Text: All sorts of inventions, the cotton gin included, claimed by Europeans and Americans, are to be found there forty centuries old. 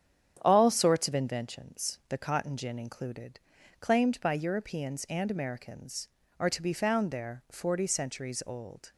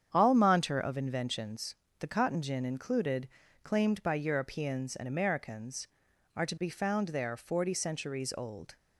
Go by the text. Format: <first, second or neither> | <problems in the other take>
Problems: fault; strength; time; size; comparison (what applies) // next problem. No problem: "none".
first | starts louder than the rest; strong; until 1.1 s; 8 dB; strong in the first // says "monter" for "sorts"; at 0.3 s